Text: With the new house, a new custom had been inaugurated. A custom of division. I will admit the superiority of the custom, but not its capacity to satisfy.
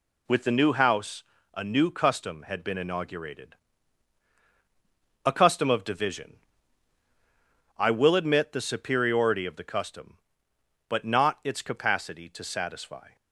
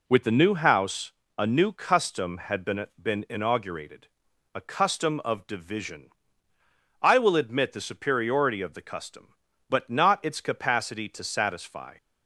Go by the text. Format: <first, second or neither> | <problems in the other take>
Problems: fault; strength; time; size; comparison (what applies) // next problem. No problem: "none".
first | says "been" twice; at 3.0 s